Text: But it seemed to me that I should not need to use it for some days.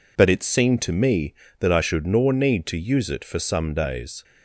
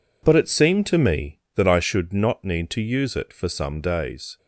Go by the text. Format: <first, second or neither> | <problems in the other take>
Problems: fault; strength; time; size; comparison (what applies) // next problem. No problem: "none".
second | says "nor" for "not"; at 2.0 s